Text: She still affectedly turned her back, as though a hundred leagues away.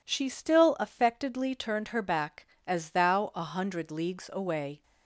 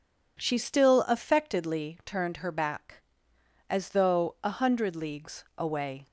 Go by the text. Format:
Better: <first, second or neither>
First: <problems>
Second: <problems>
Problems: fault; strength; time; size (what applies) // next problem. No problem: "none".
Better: second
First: says "thou" for "though"; at 2.9 s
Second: none